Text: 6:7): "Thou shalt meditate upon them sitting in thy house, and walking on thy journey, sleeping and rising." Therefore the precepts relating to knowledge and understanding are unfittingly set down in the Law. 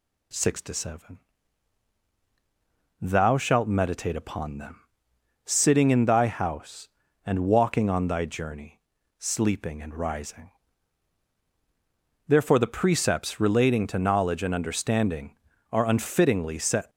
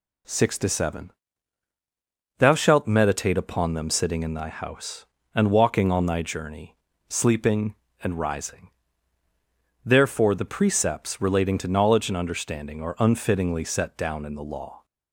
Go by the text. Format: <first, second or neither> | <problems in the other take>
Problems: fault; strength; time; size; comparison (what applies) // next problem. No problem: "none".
second | pauses between "them" and "sitting"; noticeable; at 4.7 s; 0.64 s long // stops before "down in the Law"; at 16.9 s